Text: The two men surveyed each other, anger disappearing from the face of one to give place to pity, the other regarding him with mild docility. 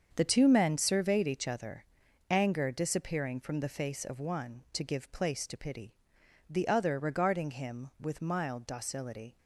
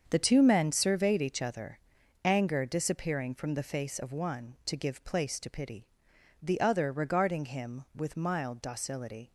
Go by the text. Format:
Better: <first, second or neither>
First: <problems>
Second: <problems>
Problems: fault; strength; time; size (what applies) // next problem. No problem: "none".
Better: neither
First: starts louder than the rest; strong; until 1.1 s; 7 dB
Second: starts louder than the rest; strong; until 1.1 s; 7 dB